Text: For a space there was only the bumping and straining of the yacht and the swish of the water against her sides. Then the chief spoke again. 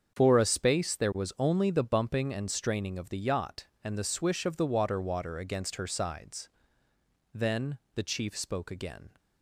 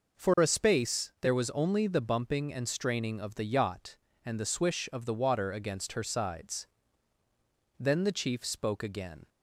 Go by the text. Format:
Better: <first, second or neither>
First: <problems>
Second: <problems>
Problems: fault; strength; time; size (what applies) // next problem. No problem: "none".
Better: second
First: starts louder than the rest; strong; until 1.1 s; 7 dB // says "water" twice; at 4.9 s // pauses between "Then" and "the"; slight; at 7.7 s; 0.20 s long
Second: none